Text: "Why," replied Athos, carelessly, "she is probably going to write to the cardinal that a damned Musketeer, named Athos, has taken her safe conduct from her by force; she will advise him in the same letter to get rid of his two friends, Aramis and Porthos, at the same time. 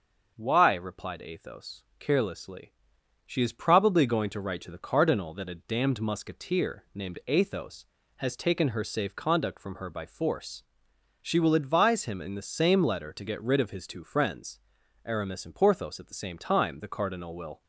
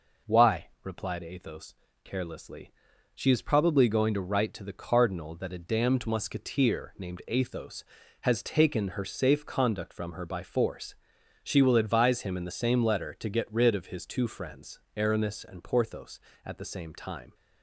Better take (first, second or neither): second